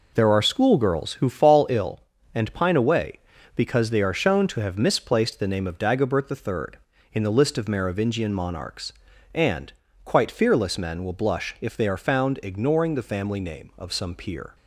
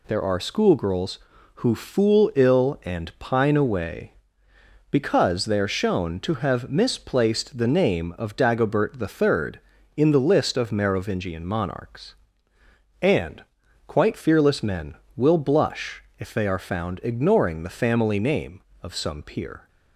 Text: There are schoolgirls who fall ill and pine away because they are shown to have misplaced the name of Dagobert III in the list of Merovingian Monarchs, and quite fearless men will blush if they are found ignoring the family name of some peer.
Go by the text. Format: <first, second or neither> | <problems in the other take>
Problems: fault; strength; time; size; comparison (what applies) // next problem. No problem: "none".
first | says "fool" for "fall"; at 1.7 s // pauses between "and" and "quite"; at 13.4 s; 0.44 s long; slight in the first // pauses between "blush" and "if"; slight; at 16.0 s; 0.16 s long